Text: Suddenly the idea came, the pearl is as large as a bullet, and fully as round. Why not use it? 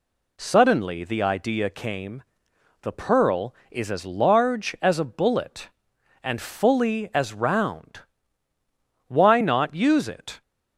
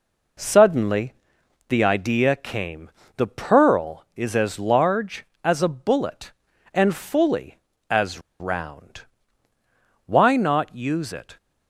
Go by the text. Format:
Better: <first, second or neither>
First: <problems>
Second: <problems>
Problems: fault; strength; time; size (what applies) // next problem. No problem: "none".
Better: first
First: none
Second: pauses between "Suddenly" and "the"; noticeable; at 1.1 s; 0.54 s long // pauses between "as" and "round"; slight; at 8.2 s; 0.19 s long